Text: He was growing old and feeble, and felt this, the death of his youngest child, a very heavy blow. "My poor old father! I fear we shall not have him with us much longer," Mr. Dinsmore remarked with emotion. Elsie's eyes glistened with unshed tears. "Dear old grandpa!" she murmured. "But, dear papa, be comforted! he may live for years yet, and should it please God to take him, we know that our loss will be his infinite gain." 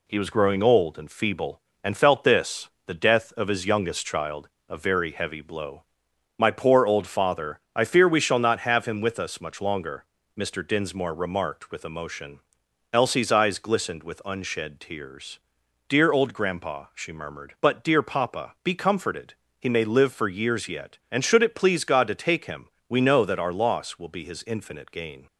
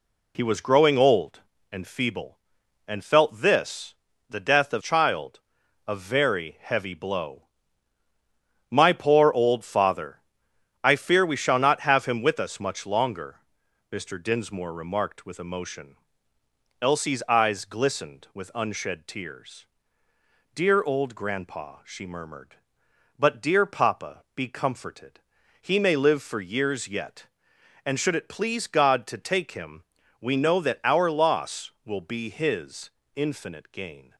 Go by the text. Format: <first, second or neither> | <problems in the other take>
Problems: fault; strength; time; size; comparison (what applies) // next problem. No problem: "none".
first | skips "his youngest"; at 4.8 s // pauses between "his" and "infinite"; slight; at 32.8 s; 0.24 s long